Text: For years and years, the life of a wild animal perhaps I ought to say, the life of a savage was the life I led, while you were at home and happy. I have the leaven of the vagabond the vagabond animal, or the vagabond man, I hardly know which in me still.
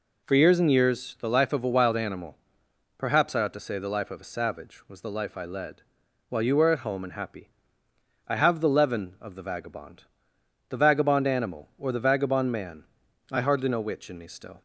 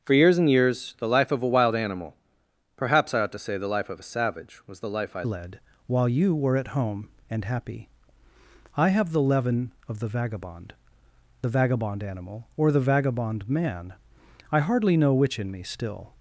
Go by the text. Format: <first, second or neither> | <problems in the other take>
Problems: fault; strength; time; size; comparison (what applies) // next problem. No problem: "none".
first | starts louder than the rest; until 1.0 s; 6.5 dB // pauses between "animal" and "perhaps"; noticeable; at 2.1 s; 0.60 s long; noticeable in the first // changes voice at "led"; from 5.2 s on; 10.9 s long // pauses between "vagabond" and "the"; noticeable; at 10.7 s; 0.68 s long; noticeable in the first